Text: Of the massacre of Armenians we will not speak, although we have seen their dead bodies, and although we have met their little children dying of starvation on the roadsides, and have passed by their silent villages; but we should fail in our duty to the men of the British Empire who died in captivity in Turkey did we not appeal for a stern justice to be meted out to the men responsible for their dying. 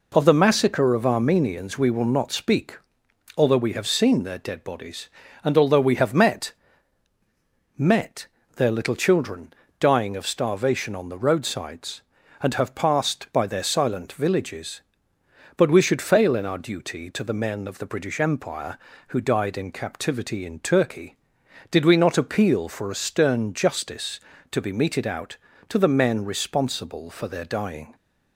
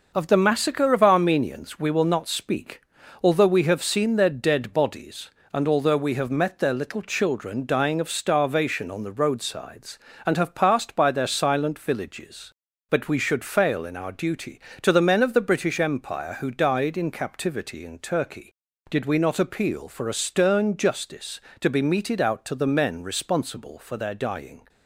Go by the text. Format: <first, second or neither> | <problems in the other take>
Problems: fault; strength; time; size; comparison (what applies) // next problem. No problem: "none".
second | says "met" twice; at 7.7 s // pauses between "children" and "dying"; slight; at 9.5 s; 0.24 s long